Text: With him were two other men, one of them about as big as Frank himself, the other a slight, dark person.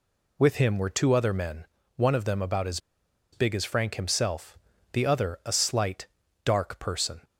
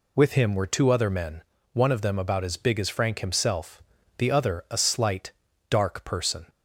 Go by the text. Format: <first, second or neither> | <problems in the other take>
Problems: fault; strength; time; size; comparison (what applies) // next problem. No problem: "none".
second | pauses between "as" and "big"; noticeable; at 2.7 s; 0.54 s long